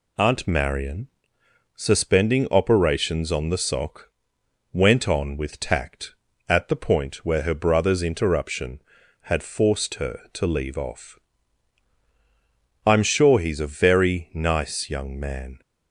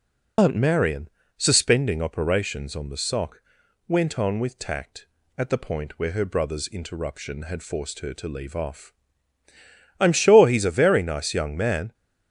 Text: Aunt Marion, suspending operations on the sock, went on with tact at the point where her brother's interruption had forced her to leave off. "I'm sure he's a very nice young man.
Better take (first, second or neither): first